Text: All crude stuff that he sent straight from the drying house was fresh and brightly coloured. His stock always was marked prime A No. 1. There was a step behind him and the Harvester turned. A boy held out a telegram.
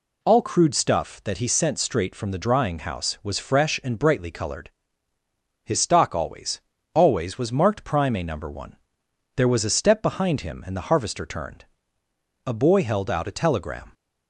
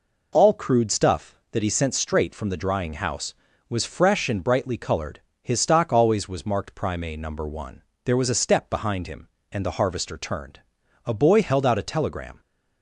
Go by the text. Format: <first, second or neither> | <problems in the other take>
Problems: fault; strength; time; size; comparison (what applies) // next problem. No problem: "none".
second | says "always" twice; at 6.9 s